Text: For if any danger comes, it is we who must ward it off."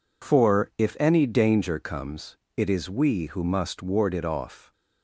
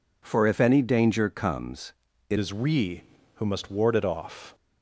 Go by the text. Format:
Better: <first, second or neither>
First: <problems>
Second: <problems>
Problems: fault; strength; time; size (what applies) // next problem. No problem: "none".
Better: first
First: none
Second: changes voice at "is"; from 2.3 s on; 2.2 s long